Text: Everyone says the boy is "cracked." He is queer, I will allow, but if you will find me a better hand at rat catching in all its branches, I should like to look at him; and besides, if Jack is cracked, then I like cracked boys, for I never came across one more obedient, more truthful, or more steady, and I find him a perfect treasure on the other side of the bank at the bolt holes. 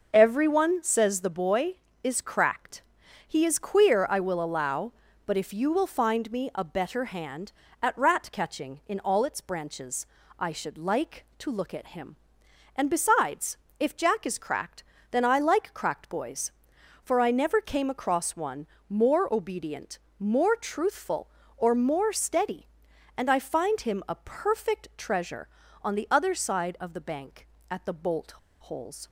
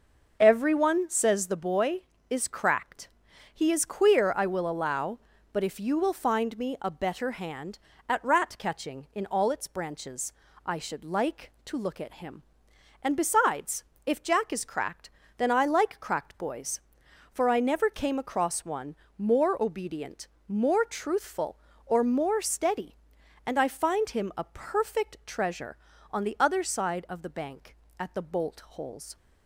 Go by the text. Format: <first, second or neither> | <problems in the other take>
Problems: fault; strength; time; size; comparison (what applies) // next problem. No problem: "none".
second | starts louder than the rest; until 1.1 s; 6 dB; also in the second // pauses between "one" and "more"; slight; at 18.6 s; 0.22 s long; slight in the second // pauses between "bolt" and "holes"; slight; at 28.3 s; 0.33 s long